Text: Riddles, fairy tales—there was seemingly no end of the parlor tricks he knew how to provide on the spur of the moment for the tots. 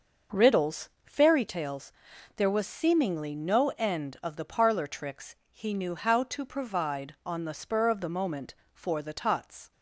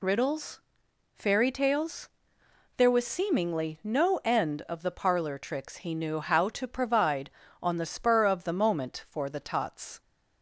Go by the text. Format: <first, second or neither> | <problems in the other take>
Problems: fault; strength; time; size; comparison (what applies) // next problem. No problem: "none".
second | starts louder than the rest; noticeable; until 1.4 s; 6 dB // pauses between "tricks" and "he"; slight; at 5.3 s; 0.16 s long